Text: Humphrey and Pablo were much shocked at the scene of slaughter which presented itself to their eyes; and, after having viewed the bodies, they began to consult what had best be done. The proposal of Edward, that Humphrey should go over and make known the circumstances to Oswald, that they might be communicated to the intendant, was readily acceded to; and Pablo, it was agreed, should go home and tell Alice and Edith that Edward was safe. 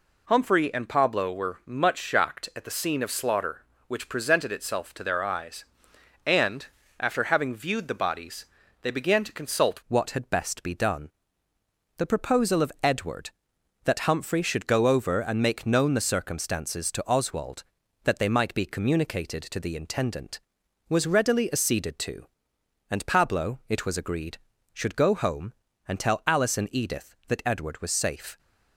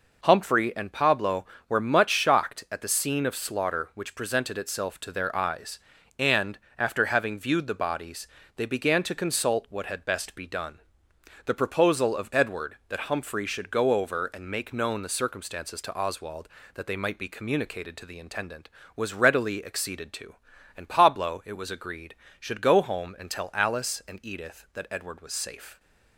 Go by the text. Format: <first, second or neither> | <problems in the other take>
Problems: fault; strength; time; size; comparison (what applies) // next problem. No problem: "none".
second | changes voice at "what"; from 9.8 s on; 18.5 s long